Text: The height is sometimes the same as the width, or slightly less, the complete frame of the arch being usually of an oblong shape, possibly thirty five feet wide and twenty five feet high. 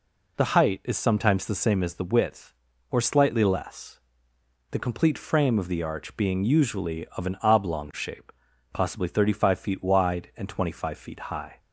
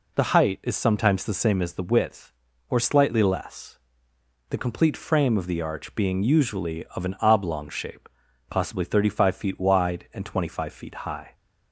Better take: neither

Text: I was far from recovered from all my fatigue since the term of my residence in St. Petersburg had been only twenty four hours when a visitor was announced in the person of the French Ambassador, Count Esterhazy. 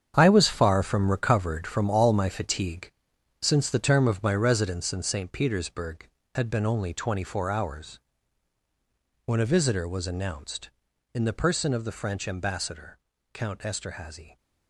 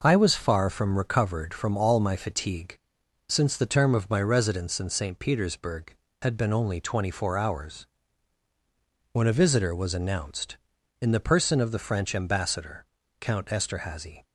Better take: second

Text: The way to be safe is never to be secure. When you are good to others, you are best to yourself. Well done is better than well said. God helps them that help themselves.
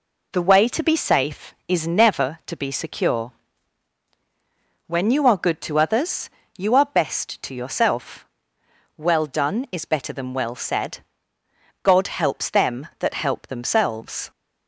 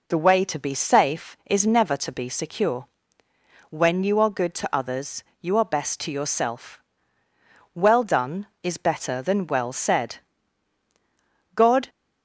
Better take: first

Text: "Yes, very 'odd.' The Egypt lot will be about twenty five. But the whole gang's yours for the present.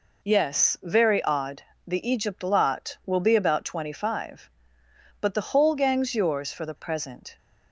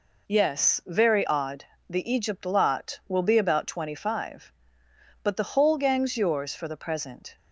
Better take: neither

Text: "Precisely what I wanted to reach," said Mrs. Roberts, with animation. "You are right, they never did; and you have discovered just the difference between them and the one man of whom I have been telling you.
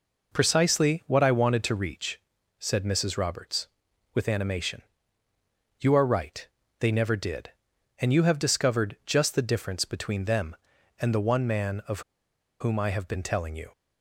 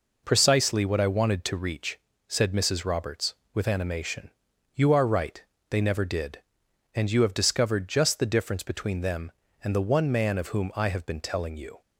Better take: second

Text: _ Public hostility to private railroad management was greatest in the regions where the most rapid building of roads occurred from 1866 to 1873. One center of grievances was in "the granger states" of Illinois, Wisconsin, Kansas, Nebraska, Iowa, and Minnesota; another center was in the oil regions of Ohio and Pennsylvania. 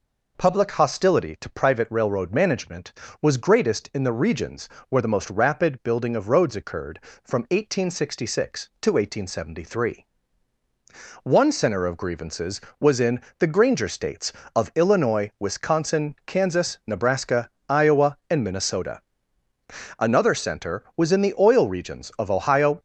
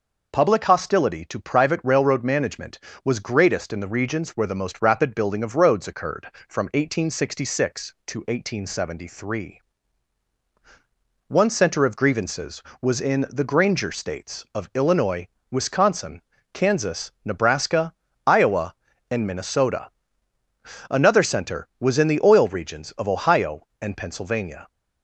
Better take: second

